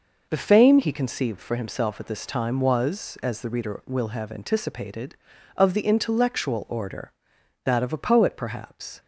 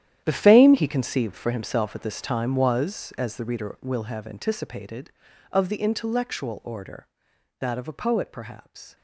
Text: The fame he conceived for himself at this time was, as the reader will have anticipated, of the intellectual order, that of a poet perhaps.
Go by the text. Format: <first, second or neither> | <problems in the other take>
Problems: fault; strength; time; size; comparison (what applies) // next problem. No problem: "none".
first | gets quieter; strong; throughout; 14 dB